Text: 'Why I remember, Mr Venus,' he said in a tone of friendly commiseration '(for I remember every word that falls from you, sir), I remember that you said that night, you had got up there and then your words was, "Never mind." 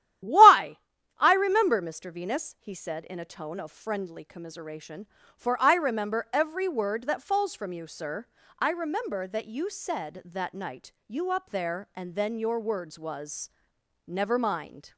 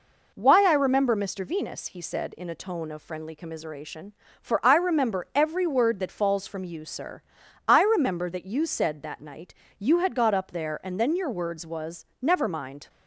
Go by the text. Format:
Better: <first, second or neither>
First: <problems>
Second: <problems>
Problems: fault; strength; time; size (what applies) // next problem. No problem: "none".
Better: second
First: starts louder than the rest; strong; until 1.6 s; 12 dB // pauses between "Why" and "I"; at 0.7 s; 0.40 s long // skips "had got"; at 11.2 s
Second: none